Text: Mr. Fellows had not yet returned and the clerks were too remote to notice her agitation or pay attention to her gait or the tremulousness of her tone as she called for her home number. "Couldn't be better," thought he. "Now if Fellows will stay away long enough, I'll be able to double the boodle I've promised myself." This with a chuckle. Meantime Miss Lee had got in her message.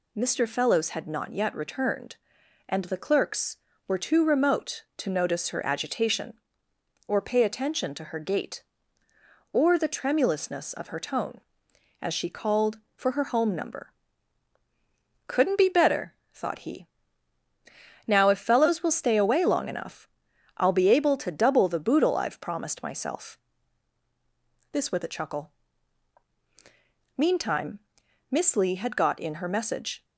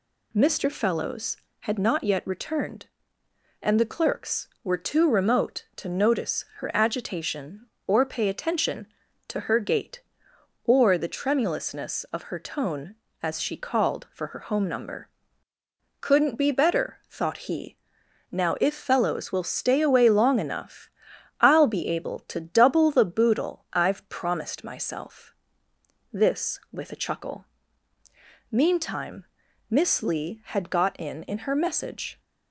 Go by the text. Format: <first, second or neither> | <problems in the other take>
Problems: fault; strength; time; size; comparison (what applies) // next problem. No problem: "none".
first | pauses between "Meantime" and "Miss"; at 29.2 s; 0.44 s long; noticeable in the first // says "in" twice; at 31.2 s